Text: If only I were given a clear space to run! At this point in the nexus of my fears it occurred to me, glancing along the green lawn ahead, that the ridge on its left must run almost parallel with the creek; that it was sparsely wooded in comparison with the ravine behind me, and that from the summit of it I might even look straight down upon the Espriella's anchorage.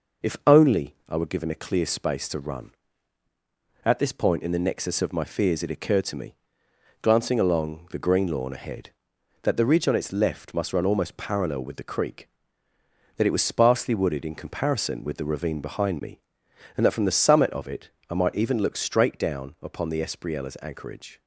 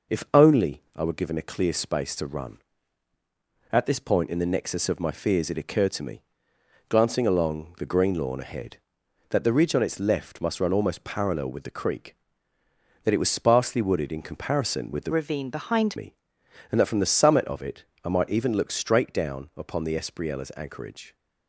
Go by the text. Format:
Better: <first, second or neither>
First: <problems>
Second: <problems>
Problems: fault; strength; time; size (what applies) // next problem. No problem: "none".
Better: first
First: pauses between "it" and "I"; slight; at 17.8 s; 0.20 s long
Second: changes voice from "ravine" to "behind"; from 15.1 to 15.9 s; 0.8 s long // pauses between "it" and "I"; slight; at 17.8 s; 0.20 s long